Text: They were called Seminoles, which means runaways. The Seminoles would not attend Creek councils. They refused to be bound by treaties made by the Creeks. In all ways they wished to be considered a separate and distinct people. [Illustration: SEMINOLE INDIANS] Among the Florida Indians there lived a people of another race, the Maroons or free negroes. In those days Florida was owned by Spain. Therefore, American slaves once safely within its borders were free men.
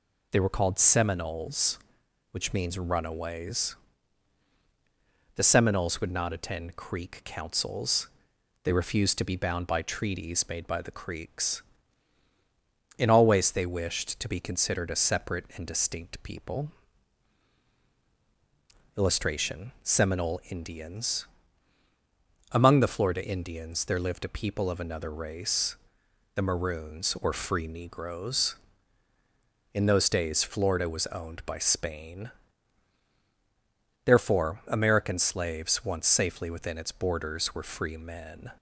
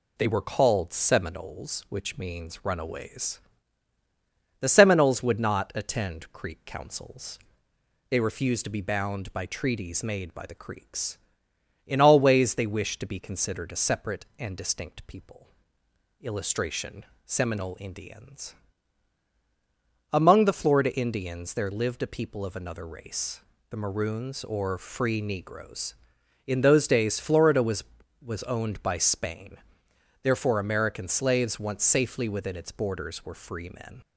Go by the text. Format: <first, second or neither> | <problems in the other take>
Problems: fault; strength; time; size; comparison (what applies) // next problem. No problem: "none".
first | pauses between "INDIANS" and "Among"; strong; at 18.5 s; 1.5 s long; also in the first // says "was" twice; at 28.2 s